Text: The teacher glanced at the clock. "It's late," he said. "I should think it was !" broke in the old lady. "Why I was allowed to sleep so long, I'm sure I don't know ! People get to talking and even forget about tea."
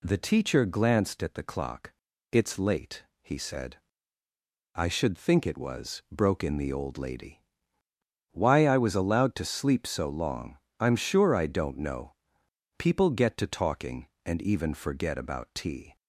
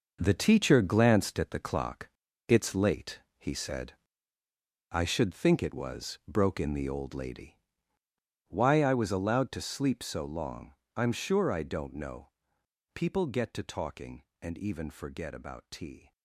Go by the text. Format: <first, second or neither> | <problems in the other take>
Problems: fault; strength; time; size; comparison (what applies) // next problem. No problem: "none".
first | gets quieter; strong; throughout; 9.5 dB